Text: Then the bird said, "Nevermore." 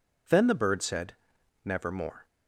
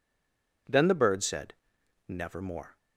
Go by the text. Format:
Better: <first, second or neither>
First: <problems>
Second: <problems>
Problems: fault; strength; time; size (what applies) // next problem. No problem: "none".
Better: first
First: none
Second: stays silent before the first word; slight; until 0.6 s; 0.6 s long